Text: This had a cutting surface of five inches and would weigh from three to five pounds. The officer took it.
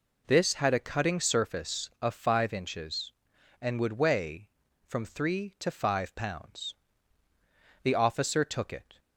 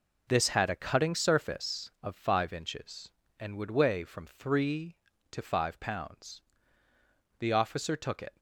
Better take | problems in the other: neither | none

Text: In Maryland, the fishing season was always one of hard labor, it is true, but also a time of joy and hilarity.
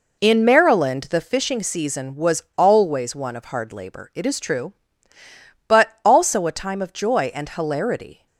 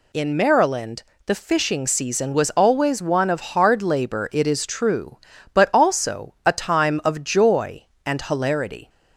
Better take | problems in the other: second | starts louder than the rest; noticeable; until 1.2 s; 4 dB // pauses between "was" and "always"; slight; at 2.4 s; 0.15 s long

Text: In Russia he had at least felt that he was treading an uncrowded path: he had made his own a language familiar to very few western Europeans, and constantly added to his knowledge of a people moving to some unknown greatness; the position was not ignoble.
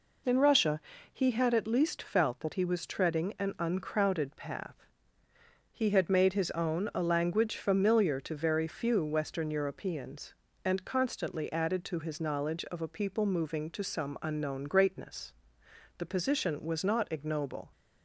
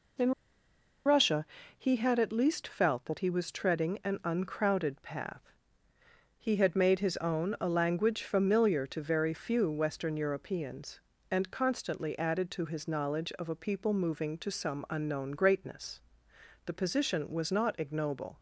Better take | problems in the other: first | pauses between "In" and "Russia"; noticeable; at 0.3 s; 0.75 s long // pauses between "Russia" and "he"; slight; at 1.4 s; 0.32 s long; slight in the first

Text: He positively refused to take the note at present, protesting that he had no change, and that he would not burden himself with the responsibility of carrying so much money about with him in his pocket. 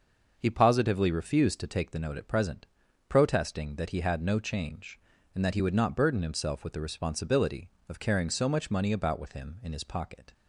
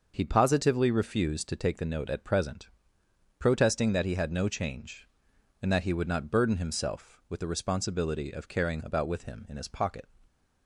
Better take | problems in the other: first | starts louder than the rest; noticeable; until 1.1 s; 6 dB; noticeable in the first // skips "so much money"; at 8.8 s

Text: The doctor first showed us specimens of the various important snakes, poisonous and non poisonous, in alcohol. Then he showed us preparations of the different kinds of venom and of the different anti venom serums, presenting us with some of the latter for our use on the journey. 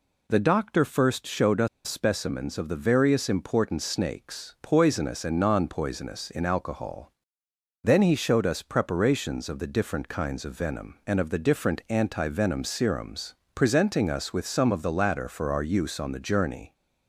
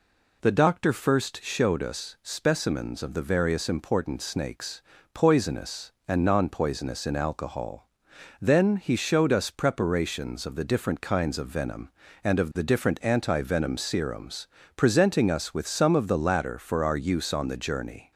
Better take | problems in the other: second | pauses between "us" and "specimens"; slight; at 1.6 s; 0.19 s long

